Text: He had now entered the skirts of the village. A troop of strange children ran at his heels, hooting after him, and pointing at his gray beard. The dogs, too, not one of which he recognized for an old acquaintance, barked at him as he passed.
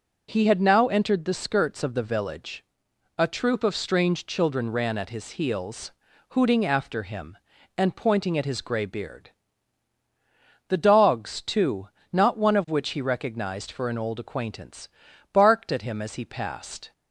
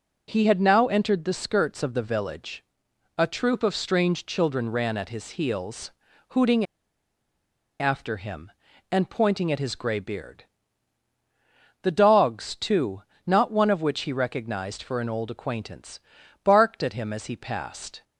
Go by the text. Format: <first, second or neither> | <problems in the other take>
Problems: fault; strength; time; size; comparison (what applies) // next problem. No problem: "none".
first | pauses between "hooting" and "after"; at 6.6 s; 1.1 s long